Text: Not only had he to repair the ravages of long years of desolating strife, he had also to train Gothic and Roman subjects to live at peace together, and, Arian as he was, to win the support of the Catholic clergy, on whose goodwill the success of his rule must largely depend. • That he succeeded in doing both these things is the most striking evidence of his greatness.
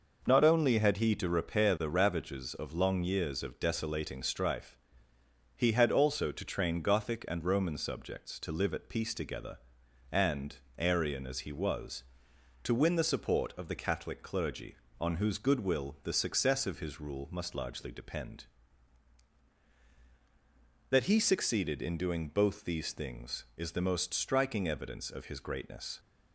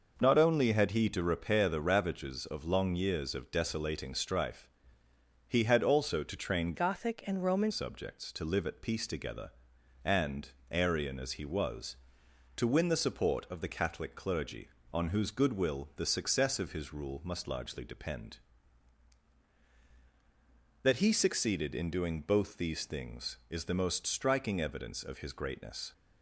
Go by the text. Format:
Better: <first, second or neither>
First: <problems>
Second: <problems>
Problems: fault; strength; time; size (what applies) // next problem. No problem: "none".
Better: first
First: none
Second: changes voice from "Gothic" to "Roman"; from 6.7 to 7.7 s; 1.0 s long